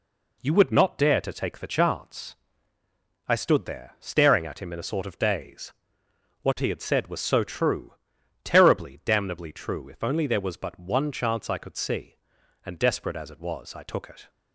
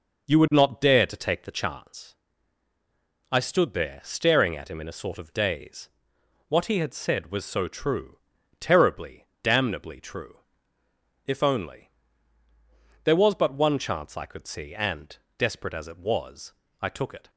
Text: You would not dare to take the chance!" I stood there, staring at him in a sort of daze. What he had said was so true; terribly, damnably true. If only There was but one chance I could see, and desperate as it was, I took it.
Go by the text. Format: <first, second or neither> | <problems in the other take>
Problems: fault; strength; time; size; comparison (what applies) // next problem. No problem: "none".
first | starts louder than the rest; noticeable; until 2.0 s; 5.5 dB // pauses between "only" and "There"; at 11.9 s; 1.1 s long // pauses between "and" and "desperate"; slight; at 15.1 s; 0.22 s long